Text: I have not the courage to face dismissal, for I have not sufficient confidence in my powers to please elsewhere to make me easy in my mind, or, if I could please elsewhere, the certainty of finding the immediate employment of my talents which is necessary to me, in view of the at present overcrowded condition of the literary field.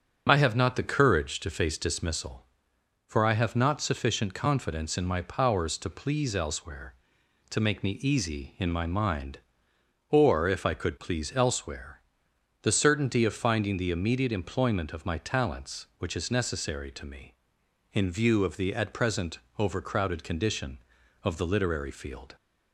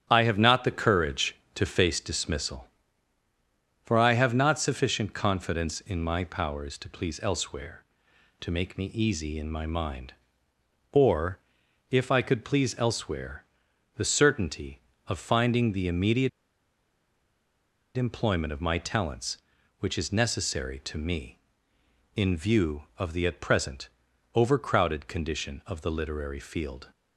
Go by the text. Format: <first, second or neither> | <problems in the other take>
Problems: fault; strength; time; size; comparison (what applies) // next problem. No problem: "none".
first | starts louder than the rest; strong; until 1.1 s; 10 dB; also in the first // pauses between "immediate" and "employment"; strong; at 16.2 s; 1.6 s long // pauses between "present" and "overcrowded"; noticeable; at 23.8 s; 0.46 s long; slight in the first